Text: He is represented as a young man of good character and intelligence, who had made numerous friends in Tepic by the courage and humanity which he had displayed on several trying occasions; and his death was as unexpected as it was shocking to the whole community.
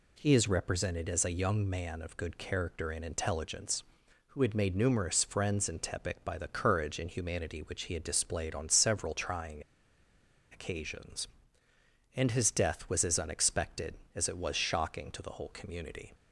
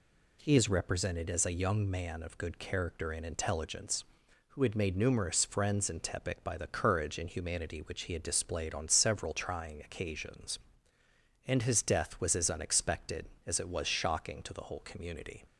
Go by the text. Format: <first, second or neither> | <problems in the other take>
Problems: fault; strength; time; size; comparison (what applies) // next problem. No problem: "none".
second | pauses between "trying" and "occasions"; noticeable; at 9.6 s; 0.90 s long